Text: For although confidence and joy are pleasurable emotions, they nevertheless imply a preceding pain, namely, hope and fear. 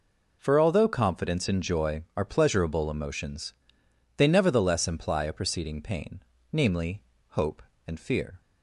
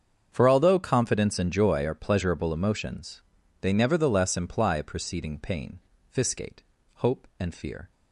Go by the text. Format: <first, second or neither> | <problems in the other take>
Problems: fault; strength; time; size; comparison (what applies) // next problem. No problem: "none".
first | starts louder than the rest; strong; until 1.3 s; 7 dB // says "fiscate" for "namely"; at 6.0 s